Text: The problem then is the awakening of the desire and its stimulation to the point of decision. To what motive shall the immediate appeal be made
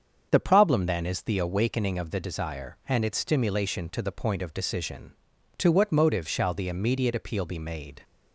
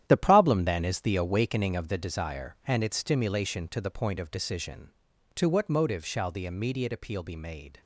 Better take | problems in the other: first | gets quieter; strong; throughout; 11 dB // starts louder than the rest; strong; until 1.1 s; 11 dB; also in the first

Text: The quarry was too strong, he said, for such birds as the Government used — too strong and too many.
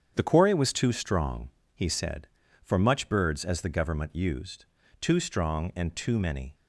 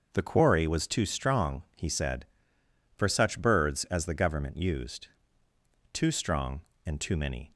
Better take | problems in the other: second | starts louder than the rest; strong; until 1.1 s; 8 dB; also in the second // says "much" for "such"; at 2.7 s

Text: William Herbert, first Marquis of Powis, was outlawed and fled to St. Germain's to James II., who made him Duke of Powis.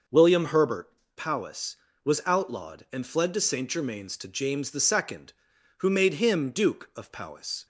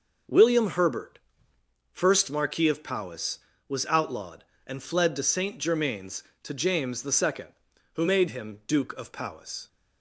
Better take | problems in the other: second | skips "first Marquis of"; at 1.0 s

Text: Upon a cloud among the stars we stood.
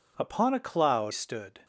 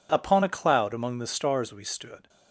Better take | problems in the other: second | skips "among the stars we"; at 1.1 s

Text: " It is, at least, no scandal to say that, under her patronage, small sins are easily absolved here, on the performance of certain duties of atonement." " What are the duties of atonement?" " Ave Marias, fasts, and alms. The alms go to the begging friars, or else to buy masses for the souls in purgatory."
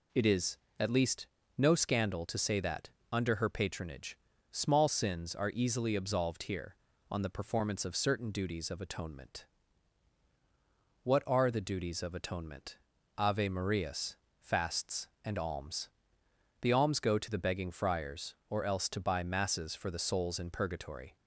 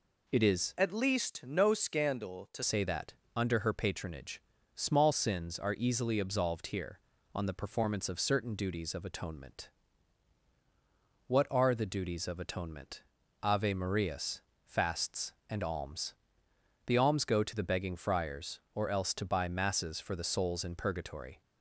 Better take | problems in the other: first | changes voice from "at" to "to"; from 0.7 to 2.6 s; 1.9 s long

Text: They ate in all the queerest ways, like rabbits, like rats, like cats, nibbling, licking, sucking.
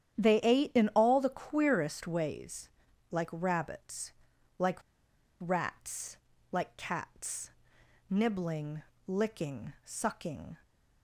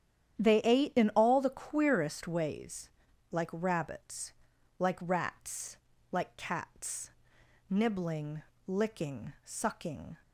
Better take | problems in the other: second | starts louder than the rest; strong; until 1.3 s; 10 dB; strong in the second // pauses between "like" and "rats"; noticeable; at 4.7 s; 0.63 s long

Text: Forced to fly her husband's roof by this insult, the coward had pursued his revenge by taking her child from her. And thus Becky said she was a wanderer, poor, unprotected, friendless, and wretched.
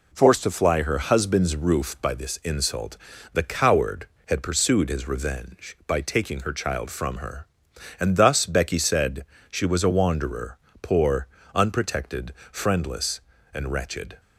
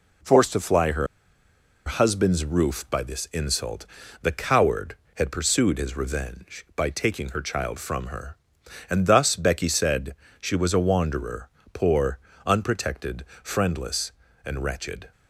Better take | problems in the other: first | pauses between "her" and "husband's"; noticeable; at 1.0 s; 0.80 s long // pauses between "said" and "she"; slight; at 10.1 s; 0.26 s long; slight in the first

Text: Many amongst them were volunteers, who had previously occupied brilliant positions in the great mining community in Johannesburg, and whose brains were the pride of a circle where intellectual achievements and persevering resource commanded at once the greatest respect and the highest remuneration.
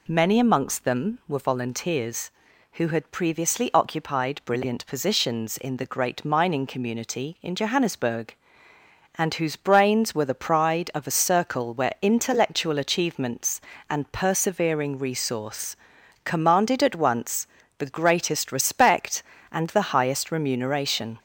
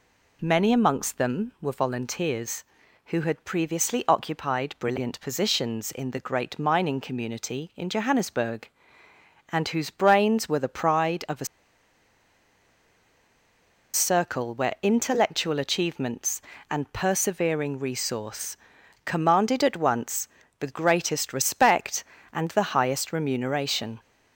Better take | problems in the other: first | pauses between "a" and "circle"; strong; at 11.4 s; 2.4 s long // pauses between "resource" and "commanded"; noticeable; at 18.5 s; 0.50 s long; noticeable in the first // pauses between "once" and "the"; slight; at 20.2 s; 0.32 s long; slight in the first

